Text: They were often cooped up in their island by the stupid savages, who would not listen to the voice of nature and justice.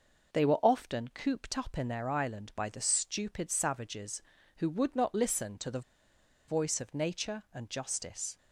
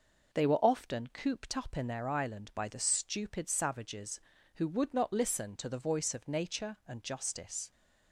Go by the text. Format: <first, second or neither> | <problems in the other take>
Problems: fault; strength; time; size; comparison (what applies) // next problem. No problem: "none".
second | pauses between "the" and "voice"; noticeable; at 5.8 s; 0.67 s long